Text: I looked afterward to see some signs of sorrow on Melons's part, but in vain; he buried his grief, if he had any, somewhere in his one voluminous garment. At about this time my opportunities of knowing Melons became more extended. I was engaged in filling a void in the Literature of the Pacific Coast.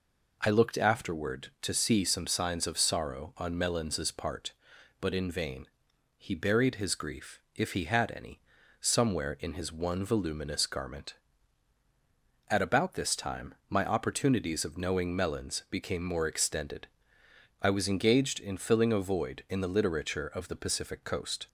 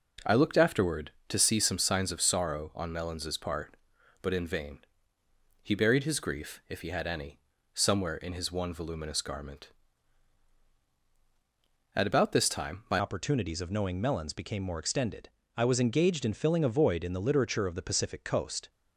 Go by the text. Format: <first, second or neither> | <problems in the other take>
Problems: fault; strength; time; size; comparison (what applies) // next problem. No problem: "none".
first | changes voice at "opportunities"; from 12.9 s on; 5.7 s long